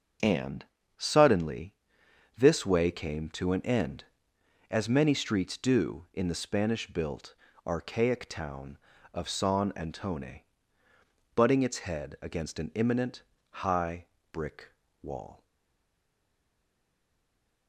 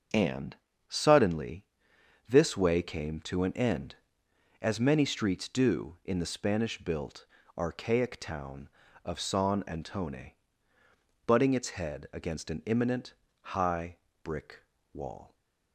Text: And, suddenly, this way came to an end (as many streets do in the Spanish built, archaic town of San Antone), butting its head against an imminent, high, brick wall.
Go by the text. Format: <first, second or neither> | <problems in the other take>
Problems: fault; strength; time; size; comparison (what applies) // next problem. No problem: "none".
second | starts louder than the rest; until 1.5 s; 6.5 dB; also in the second // pauses between "brick" and "wall"; slight; at 14.6 s; 0.32 s long; slight in the second // stays silent after the last word; from 15.4 s on; 2.2 s long